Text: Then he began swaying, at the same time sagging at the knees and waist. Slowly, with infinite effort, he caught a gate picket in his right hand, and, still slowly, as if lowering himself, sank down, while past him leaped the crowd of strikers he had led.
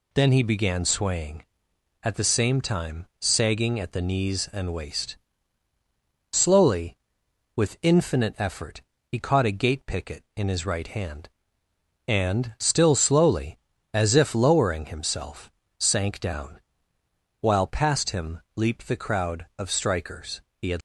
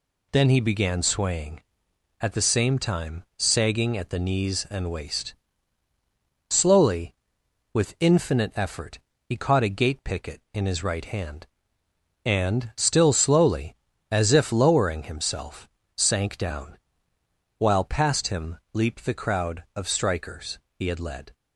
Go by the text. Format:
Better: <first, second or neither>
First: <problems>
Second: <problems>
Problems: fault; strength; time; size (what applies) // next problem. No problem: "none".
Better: second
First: pauses between "time" and "sagging"; slight; at 3.0 s; 0.16 s long // pauses between "strikers" and "he"; slight; at 20.4 s; 0.16 s long // stops before "led"; at 20.7 s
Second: pauses between "time" and "sagging"; slight; at 3.2 s; 0.16 s long // pauses between "strikers" and "he"; slight; at 20.5 s; 0.16 s long